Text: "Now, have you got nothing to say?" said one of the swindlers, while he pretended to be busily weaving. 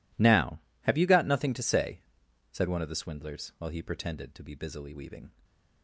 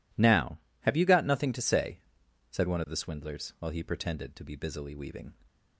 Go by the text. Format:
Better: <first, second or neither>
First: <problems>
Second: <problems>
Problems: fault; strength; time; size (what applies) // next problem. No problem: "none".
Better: second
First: gets quieter; strong; throughout; 19 dB // stays silent after the last word; slight; from 5.3 s on; 0.5 s long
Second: none